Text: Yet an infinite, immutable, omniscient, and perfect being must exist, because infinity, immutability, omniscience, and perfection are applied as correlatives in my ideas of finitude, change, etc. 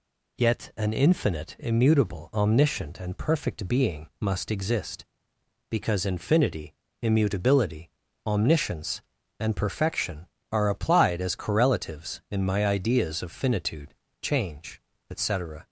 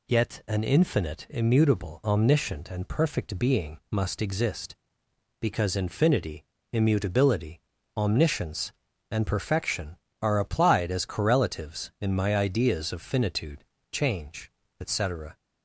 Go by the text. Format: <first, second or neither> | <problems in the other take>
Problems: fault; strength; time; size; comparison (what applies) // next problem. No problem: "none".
neither | none